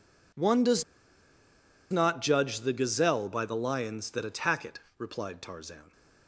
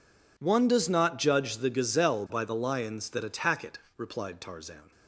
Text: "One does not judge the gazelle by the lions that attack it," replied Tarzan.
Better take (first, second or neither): second